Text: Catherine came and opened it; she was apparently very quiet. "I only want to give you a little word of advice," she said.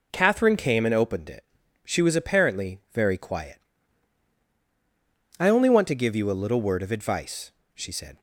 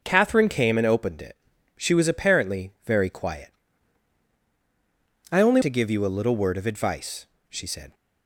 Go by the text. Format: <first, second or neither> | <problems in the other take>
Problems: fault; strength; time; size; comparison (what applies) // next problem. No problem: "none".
first | skips "want"; at 5.6 s